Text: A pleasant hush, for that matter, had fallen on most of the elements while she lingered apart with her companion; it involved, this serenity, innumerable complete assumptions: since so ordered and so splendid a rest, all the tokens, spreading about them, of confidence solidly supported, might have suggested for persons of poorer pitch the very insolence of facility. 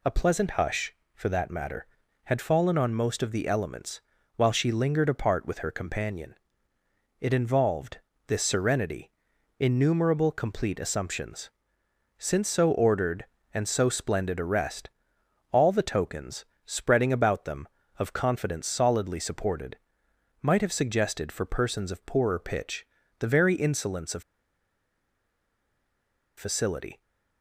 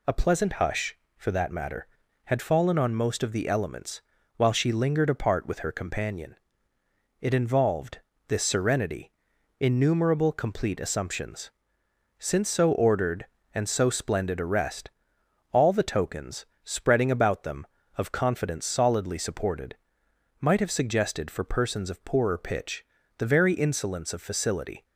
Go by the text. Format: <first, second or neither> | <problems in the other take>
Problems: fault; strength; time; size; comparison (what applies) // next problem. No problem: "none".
second | pauses between "elements" and "while"; slight; at 4.0 s; 0.36 s long; slight in the second // pauses between "pitch" and "the"; slight; at 22.8 s; 0.32 s long; slight in the second // pauses between "of" and "facility"; strong; at 24.2 s; 2.1 s long